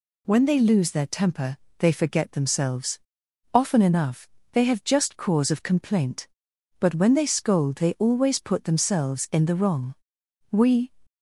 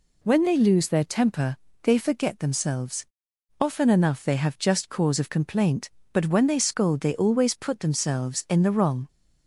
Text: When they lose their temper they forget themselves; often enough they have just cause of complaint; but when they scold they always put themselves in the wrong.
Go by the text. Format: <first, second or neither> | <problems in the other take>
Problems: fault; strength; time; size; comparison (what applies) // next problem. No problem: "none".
second | pauses between "temper" and "they"; slight; at 1.5 s; 0.24 s long; slight in the second // pauses between "enough" and "they"; slight; at 4.2 s; 0.26 s long // goes on to say "We"; slight; from 10.5 s on; 0.42 s long